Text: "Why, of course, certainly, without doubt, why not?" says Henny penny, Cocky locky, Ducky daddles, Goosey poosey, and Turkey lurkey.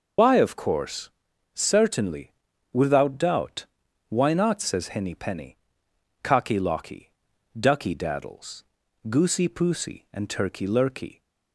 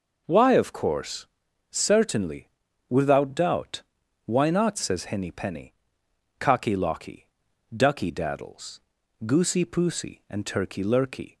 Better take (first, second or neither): second